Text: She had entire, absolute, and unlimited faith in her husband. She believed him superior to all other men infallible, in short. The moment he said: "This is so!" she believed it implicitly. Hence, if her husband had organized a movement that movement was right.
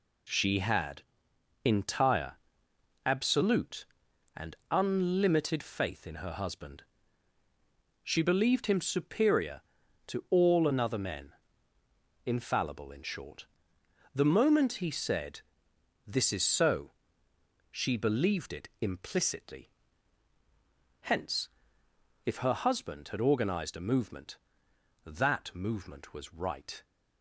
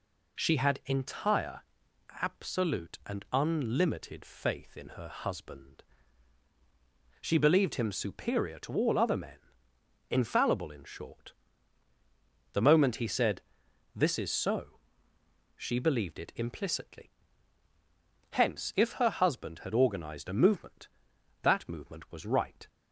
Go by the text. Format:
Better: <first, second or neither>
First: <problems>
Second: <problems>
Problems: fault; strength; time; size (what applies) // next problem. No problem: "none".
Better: second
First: pauses between "had" and "entire"; noticeable; at 1.0 s; 0.60 s long // says "another" for "other"; at 10.6 s // pauses between "men" and "infallible"; noticeable; at 11.3 s; 0.94 s long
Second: pauses between "men" and "infallible"; noticeable; at 9.3 s; 0.70 s long